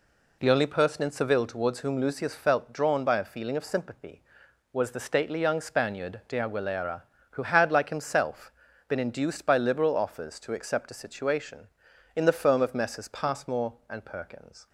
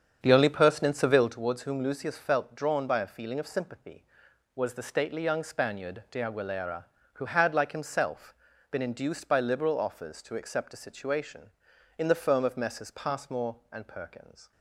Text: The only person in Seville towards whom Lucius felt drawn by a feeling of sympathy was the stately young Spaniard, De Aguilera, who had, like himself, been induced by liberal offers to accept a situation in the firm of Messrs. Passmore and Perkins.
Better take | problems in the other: first | starts louder than the rest; strong; until 1.4 s; 7.5 dB

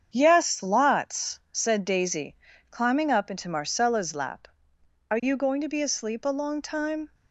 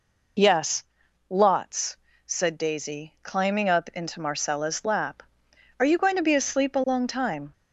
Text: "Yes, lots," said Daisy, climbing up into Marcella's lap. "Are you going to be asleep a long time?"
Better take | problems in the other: second | gets quieter; noticeable; throughout; 6 dB

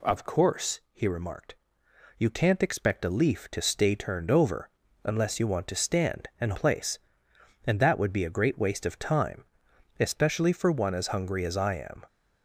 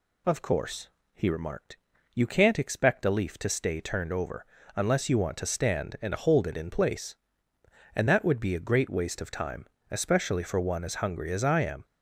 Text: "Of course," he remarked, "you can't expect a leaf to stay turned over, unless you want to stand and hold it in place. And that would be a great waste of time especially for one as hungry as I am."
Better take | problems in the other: second | skips "hold it in"; at 6.5 s // pauses between "time" and "especially"; noticeable; at 9.4 s; 0.56 s long; slight in the second

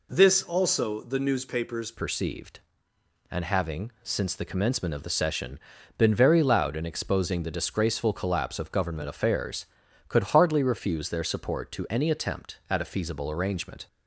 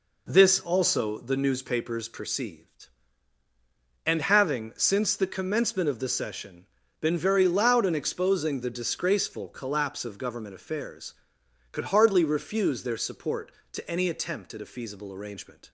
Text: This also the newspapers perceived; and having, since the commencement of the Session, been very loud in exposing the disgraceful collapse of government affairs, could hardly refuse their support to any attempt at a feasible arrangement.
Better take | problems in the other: second | changes voice at "perceived"; from 1.9 s on; 11.9 s long

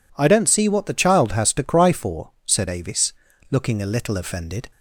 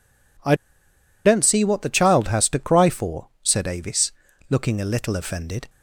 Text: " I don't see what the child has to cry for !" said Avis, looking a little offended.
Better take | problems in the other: first | pauses between "I" and "don't"; noticeable; at 0.5 s; 0.71 s long

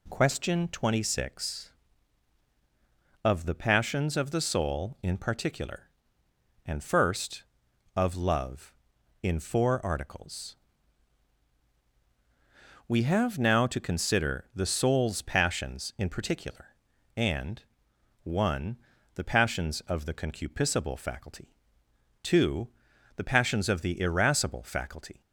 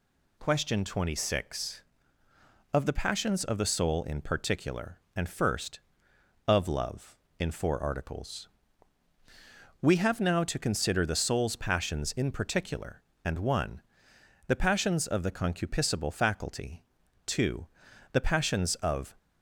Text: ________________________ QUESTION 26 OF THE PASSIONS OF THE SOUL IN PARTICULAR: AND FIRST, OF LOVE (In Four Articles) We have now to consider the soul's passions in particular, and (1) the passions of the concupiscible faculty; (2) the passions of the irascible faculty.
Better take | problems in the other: first | stops before "the irascible faculty"; at 19.1 s

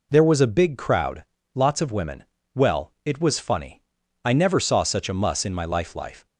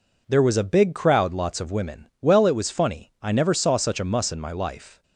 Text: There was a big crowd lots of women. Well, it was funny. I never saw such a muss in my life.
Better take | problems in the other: second | pauses between "crowd" and "lots"; slight; at 1.2 s; 0.30 s long // says "life" twice; at 5.9 s

